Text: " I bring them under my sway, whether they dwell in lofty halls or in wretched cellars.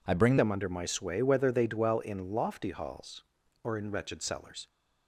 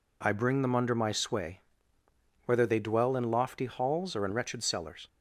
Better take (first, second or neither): second